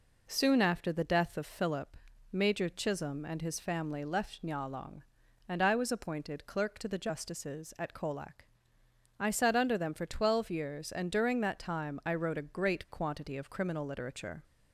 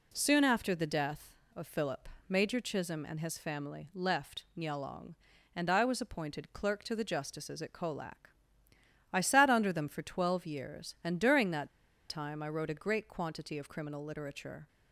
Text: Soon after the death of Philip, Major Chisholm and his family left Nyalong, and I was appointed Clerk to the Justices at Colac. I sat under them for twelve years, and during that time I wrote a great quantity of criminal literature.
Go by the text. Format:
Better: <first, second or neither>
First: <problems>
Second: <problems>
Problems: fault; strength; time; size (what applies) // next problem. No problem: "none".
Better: first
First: none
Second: pauses between "that" and "time"; at 11.6 s; 0.40 s long